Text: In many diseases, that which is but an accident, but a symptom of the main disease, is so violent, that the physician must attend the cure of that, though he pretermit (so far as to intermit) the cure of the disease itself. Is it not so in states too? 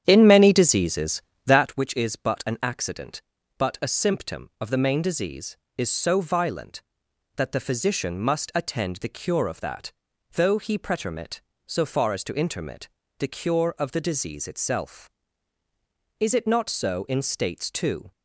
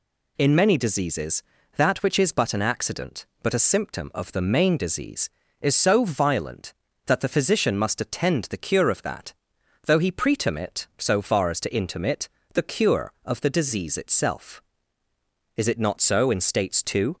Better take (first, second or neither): second